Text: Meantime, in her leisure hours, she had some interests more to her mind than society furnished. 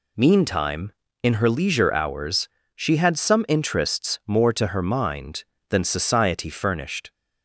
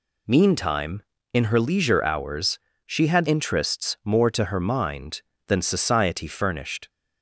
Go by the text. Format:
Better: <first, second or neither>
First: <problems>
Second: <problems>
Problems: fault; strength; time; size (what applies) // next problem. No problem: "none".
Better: first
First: none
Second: skips "some"; at 3.2 s